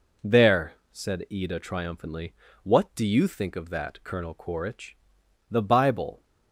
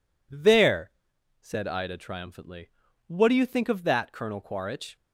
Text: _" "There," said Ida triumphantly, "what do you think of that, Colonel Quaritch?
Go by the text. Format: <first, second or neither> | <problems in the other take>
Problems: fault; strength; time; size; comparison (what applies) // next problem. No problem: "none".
second | goes on to say "The Bible"; noticeable; from 5.4 s on; 0.74 s long